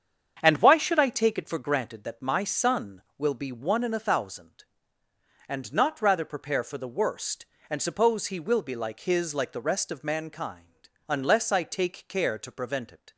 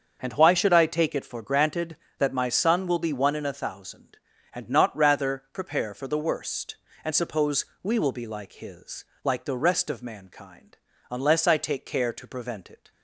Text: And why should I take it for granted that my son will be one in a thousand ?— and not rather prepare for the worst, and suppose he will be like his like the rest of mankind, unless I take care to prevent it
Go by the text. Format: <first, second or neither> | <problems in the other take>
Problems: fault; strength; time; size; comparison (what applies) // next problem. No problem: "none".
first | starts louder than the rest; until 1.2 s; 6.5 dB; strong in the first // says "we" for "he"; at 7.8 s // pauses between "his" and "like"; slight; at 9.0 s; 0.18 s long